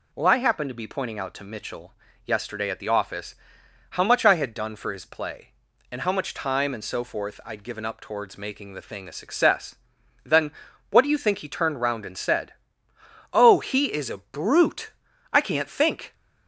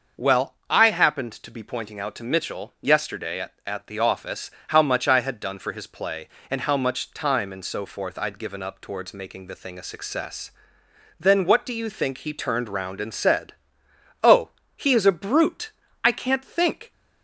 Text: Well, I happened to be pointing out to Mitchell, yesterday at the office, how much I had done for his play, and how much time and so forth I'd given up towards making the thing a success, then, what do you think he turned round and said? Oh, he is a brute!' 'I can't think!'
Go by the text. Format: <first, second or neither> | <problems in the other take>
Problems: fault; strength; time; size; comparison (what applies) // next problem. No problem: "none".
first | starts louder than the rest; until 1.3 s; 6 dB // says "at" twice; at 3.6 s